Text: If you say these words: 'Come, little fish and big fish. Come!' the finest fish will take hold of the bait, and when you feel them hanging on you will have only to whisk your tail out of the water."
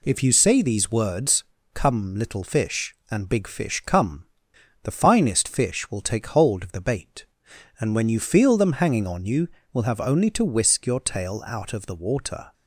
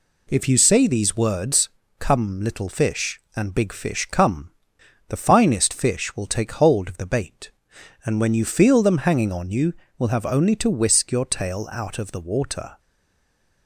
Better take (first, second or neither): first